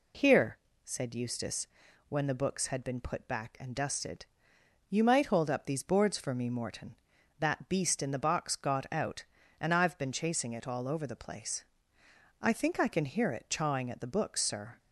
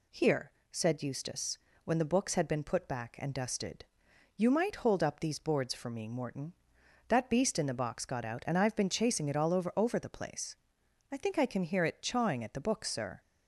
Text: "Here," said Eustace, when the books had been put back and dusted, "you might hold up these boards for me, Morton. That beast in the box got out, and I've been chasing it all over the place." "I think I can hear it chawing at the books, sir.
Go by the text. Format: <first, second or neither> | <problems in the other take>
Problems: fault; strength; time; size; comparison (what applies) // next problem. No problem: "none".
first | says "over" twice; at 9.7 s